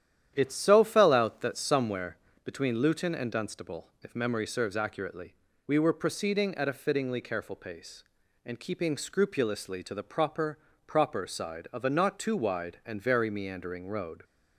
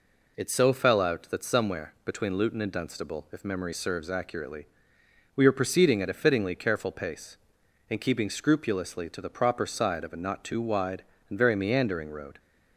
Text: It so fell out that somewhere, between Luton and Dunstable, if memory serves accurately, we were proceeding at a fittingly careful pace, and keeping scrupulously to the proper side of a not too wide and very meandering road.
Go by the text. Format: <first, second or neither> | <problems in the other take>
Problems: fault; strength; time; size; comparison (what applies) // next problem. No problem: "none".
second | starts louder than the rest; strong; until 1.3 s; 10.5 dB // says "proper" twice; at 10.8 s